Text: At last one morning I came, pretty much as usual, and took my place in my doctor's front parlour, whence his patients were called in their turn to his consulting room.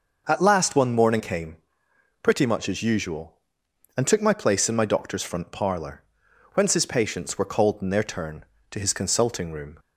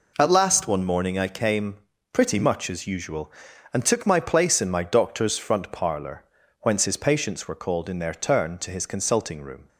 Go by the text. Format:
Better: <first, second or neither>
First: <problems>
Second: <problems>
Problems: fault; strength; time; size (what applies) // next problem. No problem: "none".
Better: second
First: skips "I"; at 1.1 s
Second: none